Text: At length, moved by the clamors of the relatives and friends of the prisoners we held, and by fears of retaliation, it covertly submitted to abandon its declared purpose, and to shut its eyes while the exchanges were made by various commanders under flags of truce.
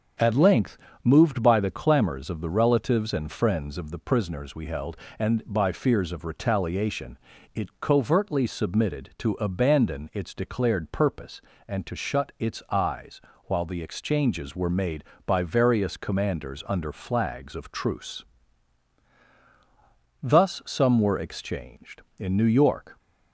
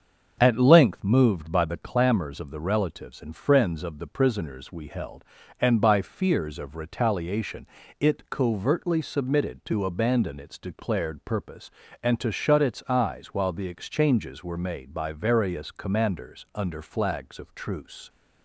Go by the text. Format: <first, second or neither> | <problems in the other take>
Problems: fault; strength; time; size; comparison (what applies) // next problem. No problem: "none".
second | starts louder than the rest; until 1.4 s; 7 dB; also in the second // pauses between "eyes" and "while"; slight; at 13.2 s; 0.24 s long // goes on to say "Thus some were exchanged in New York"; strong; from 20.2 s on; 2.7 s long